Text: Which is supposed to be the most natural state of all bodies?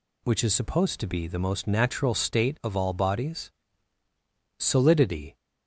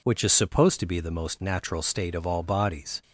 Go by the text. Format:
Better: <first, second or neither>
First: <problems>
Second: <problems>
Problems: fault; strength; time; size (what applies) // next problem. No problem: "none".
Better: second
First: goes on to say "Solidity"; noticeable; from 4.5 s on; 0.78 s long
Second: none